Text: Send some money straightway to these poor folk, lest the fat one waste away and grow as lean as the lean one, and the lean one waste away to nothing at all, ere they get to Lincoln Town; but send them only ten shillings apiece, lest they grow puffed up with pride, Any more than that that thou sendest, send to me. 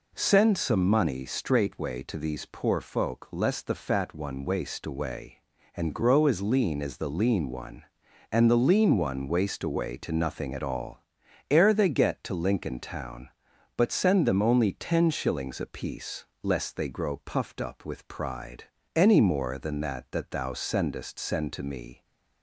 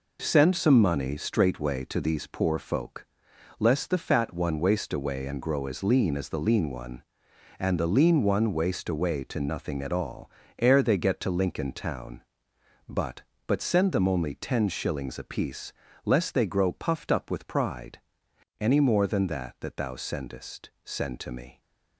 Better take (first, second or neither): first